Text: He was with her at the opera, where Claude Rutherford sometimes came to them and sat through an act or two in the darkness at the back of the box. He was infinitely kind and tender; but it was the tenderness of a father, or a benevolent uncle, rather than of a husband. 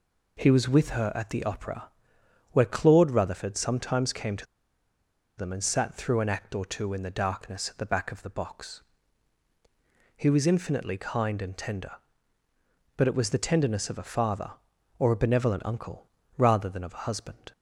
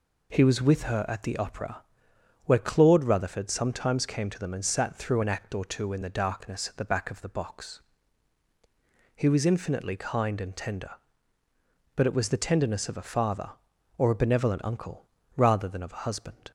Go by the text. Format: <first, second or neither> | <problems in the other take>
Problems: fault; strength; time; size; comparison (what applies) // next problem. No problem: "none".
second | pauses between "to" and "them"; noticeable; at 4.4 s; 0.92 s long